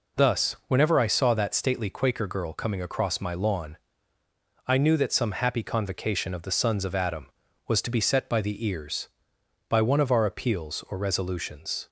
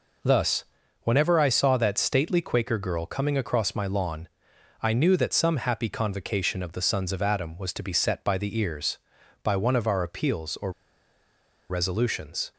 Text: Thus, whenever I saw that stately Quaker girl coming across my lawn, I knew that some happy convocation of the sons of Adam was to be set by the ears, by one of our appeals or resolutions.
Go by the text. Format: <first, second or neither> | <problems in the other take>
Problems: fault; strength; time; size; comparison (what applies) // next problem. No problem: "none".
first | pauses between "or" and "resolutions"; at 10.7 s; 0.98 s long